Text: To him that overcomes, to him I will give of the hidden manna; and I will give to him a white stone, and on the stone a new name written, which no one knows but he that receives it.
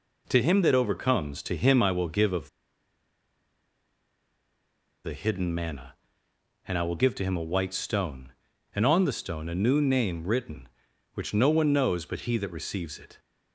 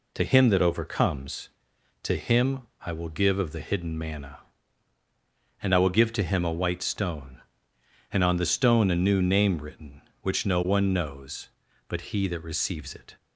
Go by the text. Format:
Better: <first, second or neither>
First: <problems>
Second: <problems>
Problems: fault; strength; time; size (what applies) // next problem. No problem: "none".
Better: second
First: pauses between "of" and "the"; strong; at 2.4 s; 2.5 s long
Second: none